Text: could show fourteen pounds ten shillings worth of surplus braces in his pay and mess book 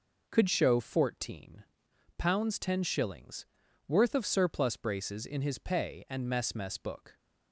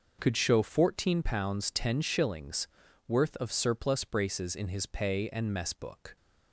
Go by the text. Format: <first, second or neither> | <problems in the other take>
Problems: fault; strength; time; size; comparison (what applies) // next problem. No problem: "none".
second | pauses between "fourteen" and "pounds"; noticeable; at 1.6 s; 0.54 s long // pauses between "shillings" and "worth"; at 3.4 s; 0.42 s long; also in the second // says "mess" twice; at 6.5 s